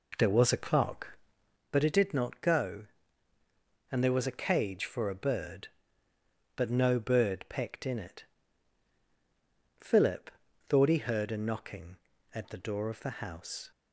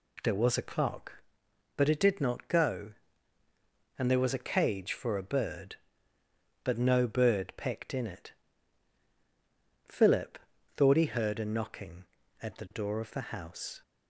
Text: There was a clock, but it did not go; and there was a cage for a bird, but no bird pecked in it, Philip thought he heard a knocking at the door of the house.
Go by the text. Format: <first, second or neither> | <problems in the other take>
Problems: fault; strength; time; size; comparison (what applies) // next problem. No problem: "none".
second | starts louder than the rest; until 1.6 s; 4 dB // pauses between "Philip" and "thought"; at 10.2 s; 0.40 s long; also in the second